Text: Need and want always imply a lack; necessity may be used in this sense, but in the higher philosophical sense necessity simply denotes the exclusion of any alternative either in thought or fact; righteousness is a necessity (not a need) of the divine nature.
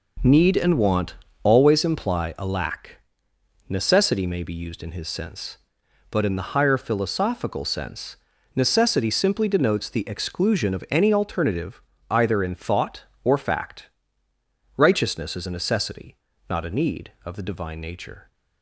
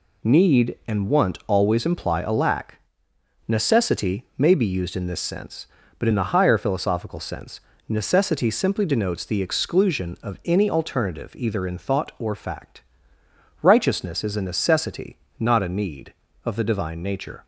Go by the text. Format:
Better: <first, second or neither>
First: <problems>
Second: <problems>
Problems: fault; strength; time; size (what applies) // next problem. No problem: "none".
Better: second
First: pauses between "want" and "always"; slight; at 1.1 s; 0.30 s long // says "his" for "this"; at 4.9 s // pauses between "sense" and "necessity"; at 8.1 s; 0.40 s long // pauses between "alternative" and "either"; slight; at 11.8 s; 0.30 s long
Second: pauses between "sense" and "necessity"; slight; at 7.6 s; 0.26 s long